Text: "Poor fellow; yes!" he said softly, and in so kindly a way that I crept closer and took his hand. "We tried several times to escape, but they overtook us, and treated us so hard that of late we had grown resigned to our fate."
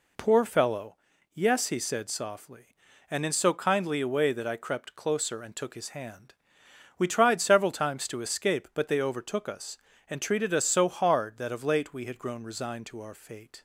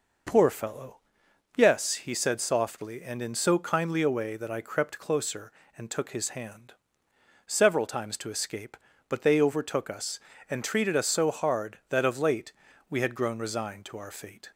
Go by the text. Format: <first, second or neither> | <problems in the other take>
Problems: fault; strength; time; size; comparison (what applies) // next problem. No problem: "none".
first | skips "We tried"; at 7.0 s // pauses between "late" and "we"; at 12.5 s; 0.38 s long